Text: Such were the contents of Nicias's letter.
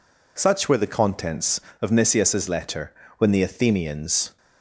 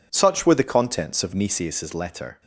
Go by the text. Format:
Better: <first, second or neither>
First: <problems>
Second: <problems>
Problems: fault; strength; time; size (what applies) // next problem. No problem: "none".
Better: second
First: goes on to say "When the Athenians"; noticeable; from 3.1 s on; 1.2 s long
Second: none